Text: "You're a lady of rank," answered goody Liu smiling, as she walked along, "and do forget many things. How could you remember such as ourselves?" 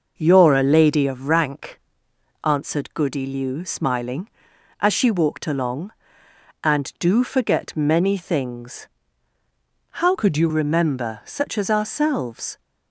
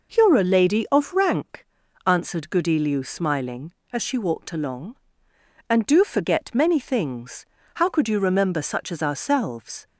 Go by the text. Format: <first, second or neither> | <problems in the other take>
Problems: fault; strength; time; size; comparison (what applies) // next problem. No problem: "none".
second | changes voice from "could" to "you"; from 10.1 to 10.4 s; 0.3 s long